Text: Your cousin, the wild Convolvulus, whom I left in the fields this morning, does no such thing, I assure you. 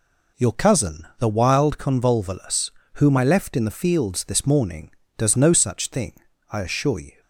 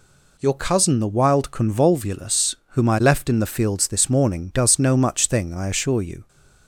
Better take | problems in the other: first | says "much" for "such"; at 4.9 s

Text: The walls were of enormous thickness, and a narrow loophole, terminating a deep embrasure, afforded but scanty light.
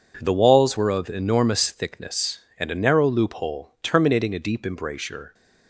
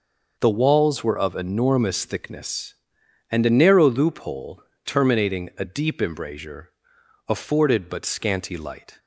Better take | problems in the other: second | stops before "afforded but scanty light"; at 5.3 s

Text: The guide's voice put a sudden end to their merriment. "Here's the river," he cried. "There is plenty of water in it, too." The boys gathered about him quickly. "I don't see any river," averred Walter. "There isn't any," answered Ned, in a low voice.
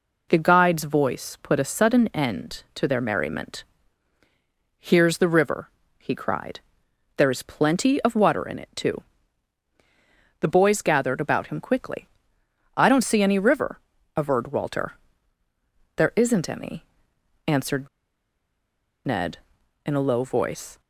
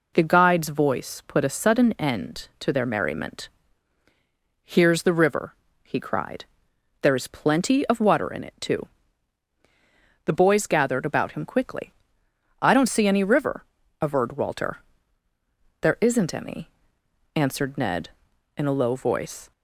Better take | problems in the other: second | pauses between "answered" and "Ned"; at 17.8 s; 1.1 s long

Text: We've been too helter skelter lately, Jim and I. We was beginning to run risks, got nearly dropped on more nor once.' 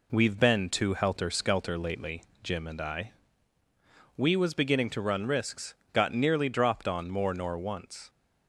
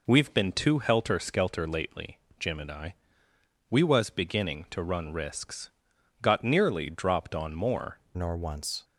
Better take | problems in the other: first | changes voice at "nor"; from 8.1 s on; 0.7 s long

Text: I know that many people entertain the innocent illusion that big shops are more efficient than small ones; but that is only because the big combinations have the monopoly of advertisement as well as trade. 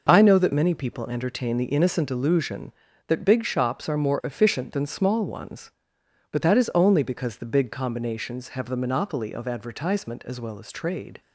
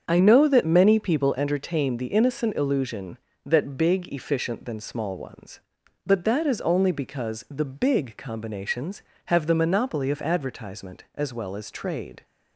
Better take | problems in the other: first | starts louder than the rest; strong; until 1.0 s; 7 dB // skips "shops are more"; at 4.1 s

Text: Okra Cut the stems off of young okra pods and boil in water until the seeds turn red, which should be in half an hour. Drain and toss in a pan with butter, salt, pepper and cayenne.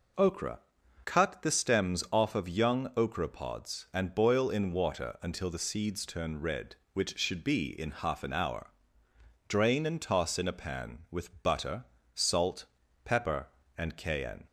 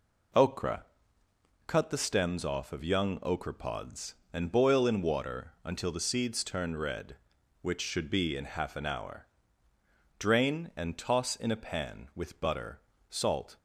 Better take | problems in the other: first | pauses between "Okra" and "Cut"; noticeable; at 0.8 s; 0.82 s long; noticeable in the first // stops before "pepper and cayenne"; at 13.5 s

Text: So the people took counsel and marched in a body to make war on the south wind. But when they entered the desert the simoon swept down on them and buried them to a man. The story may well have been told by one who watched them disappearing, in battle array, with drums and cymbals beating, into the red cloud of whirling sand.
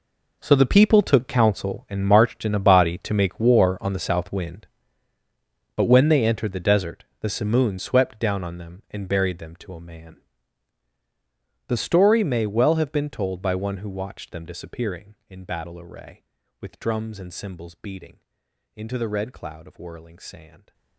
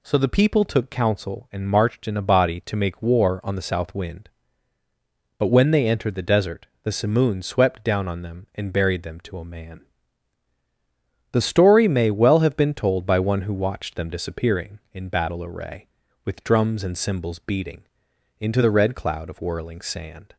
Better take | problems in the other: second | gets quieter; strong; throughout; 15 dB // pauses between "desert" and "the"; slight; at 7.0 s; 0.16 s long; slight in the second

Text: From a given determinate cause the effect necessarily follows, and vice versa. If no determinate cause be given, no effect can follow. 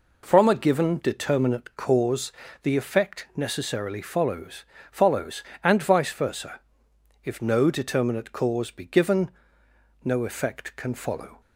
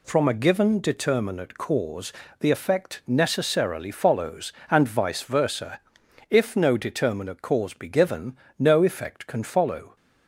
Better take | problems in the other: second | pauses between "cause" and "the"; slight; at 2.3 s; 0.30 s long; slight in the second // says "follows" twice; at 4.9 s

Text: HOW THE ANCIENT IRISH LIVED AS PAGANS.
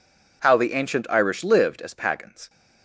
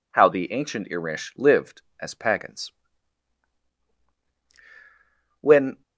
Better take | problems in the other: first | goes on to say "When"; slight; from 5.3 s on; 0.42 s long

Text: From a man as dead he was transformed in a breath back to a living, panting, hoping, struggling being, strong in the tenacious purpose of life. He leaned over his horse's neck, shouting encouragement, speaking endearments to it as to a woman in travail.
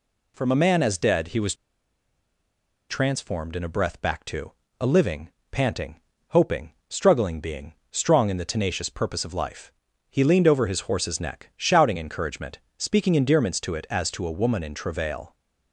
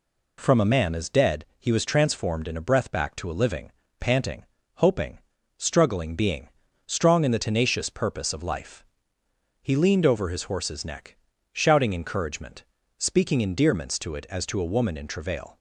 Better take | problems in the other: second | pauses between "was" and "transformed"; strong; at 1.5 s; 1.3 s long // pauses between "to" and "a"; slight; at 4.5 s; 0.28 s long

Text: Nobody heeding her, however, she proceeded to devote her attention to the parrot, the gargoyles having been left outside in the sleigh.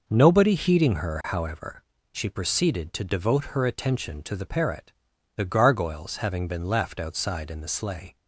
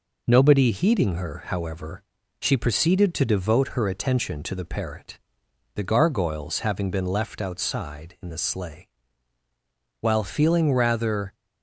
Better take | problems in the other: first | goes on to say "While feeling rather"; from 9.9 s on; 1.3 s long

